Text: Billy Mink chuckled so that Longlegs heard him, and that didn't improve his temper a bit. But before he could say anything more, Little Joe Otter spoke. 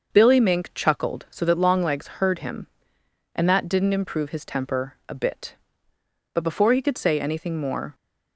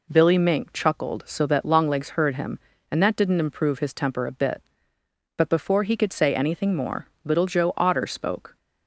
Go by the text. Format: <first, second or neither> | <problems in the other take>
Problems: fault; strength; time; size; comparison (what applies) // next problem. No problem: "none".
second | starts louder than the rest; noticeable; until 1.1 s; 6 dB // stops before "Little Joe Otter spoke"; at 7.9 s